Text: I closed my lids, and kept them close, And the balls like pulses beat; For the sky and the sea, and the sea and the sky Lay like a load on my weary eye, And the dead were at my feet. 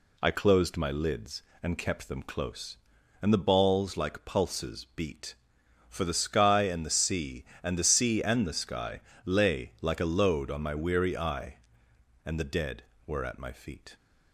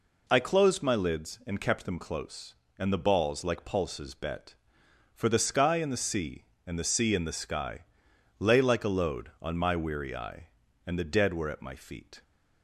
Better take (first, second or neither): first